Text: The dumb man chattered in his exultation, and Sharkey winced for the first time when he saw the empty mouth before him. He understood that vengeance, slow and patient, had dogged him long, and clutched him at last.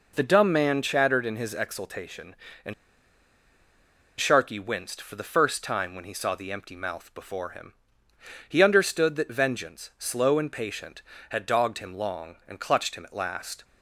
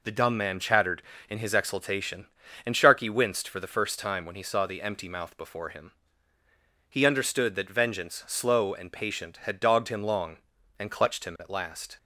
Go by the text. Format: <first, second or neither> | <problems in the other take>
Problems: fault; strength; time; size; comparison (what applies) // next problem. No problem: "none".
second | pauses between "and" and "Sharkey"; strong; at 2.7 s; 1.4 s long